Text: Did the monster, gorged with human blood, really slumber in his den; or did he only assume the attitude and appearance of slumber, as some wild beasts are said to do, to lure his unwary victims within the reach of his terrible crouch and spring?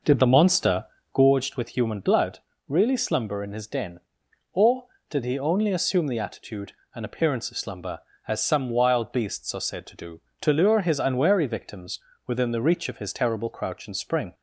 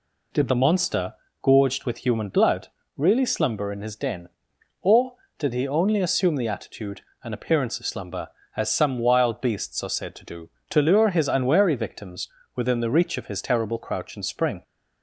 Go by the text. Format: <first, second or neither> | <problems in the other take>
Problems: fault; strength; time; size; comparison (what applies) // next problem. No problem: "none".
second | starts louder than the rest; noticeable; until 1.2 s; 5.5 dB // pauses between "victims" and "within"; slight; at 11.9 s; 0.26 s long; slight in the second